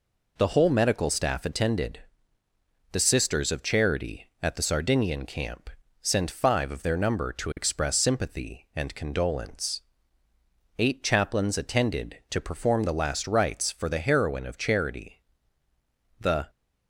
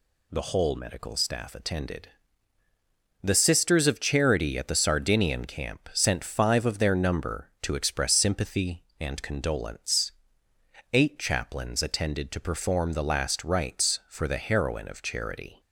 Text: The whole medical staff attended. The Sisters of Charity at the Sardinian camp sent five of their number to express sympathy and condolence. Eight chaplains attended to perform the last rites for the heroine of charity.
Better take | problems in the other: second | pauses between "camp" and "sent"; slight; at 5.6 s; 0.32 s long // goes on to say "The"; slight; from 16.1 s on; 0.30 s long

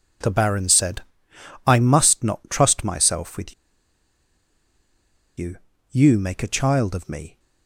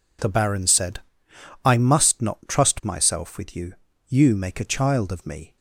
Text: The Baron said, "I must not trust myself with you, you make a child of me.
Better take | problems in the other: second | pauses between "with" and "you"; strong; at 3.5 s; 1.8 s long

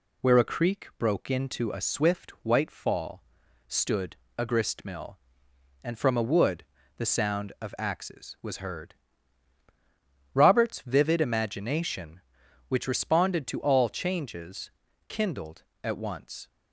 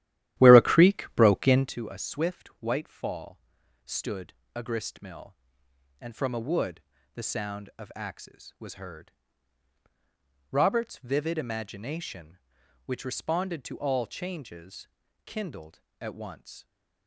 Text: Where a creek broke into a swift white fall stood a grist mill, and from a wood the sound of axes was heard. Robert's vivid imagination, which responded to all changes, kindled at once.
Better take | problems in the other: first | starts louder than the rest; strong; until 1.7 s; 13 dB // pauses between "fall" and "stood"; noticeable; at 3.3 s; 0.46 s long; noticeable in the first // pauses between "stood" and "a"; slight; at 4.3 s; 0.20 s long; slight in the first // pauses between "wood" and "the"; slight; at 6.7 s; 0.34 s long; slight in the first

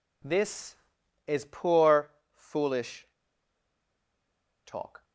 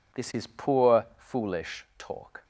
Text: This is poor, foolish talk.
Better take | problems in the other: second | pauses between "foolish" and "talk"; strong; at 3.0 s; 1.5 s long

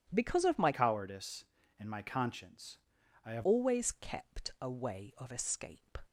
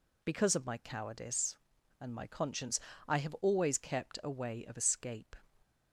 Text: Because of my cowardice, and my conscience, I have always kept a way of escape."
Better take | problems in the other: second | changes voice from "cowardice" to "have"; from 0.7 to 3.4 s; 2.7 s long

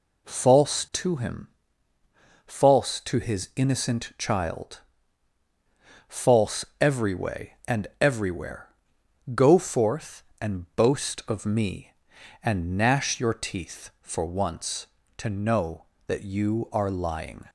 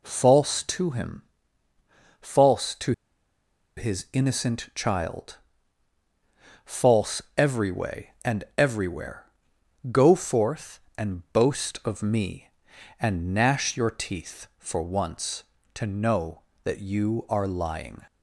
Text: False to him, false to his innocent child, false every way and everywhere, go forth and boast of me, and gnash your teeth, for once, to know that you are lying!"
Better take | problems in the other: first | pauses between "to" and "his"; noticeable; at 2.9 s; 0.85 s long // pauses between "false" and "every"; slight; at 7.1 s; 0.16 s long; slight in the first

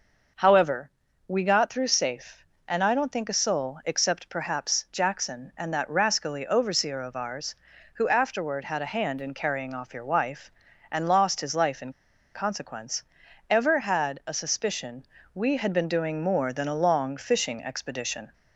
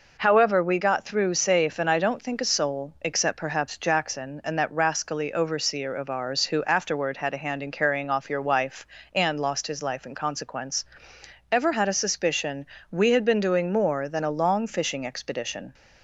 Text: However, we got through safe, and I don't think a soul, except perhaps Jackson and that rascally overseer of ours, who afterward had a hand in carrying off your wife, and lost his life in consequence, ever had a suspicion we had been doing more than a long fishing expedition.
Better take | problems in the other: second | pauses between "in" and "consequence"; at 11.9 s; 0.42 s long // pauses between "suspicion" and "we"; slight; at 15.0 s; 0.28 s long; slight in the second

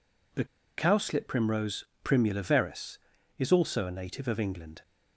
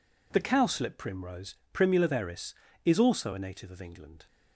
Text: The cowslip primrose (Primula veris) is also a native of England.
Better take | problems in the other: second | pauses between "The" and "cowslip"; slight; at 0.4 s; 0.33 s long

